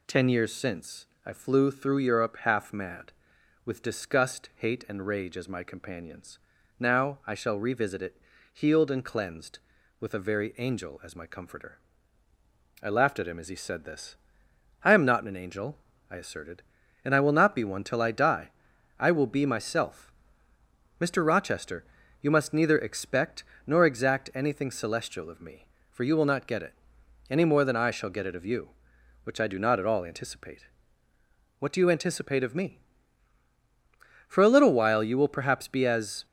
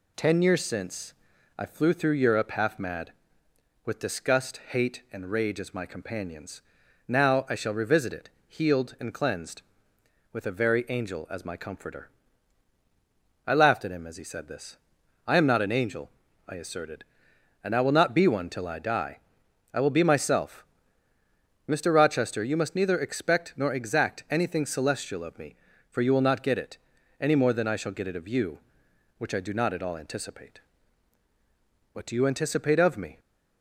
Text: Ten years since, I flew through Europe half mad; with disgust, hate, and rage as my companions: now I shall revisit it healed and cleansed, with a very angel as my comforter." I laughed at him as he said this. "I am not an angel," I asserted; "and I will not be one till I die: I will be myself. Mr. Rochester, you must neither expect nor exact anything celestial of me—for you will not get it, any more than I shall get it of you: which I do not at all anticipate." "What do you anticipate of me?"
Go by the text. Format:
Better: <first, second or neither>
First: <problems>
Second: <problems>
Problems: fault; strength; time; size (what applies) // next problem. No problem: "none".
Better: second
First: pauses between "it" and "healed"; at 8.1 s; 0.38 s long // pauses between "expect" and "nor"; slight; at 23.4 s; 0.22 s long // goes on to say "For a little while you will perhaps be as"; strong; from 34.2 s on; 1.9 s long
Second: pauses between "it" and "healed"; slight; at 8.2 s; 0.18 s long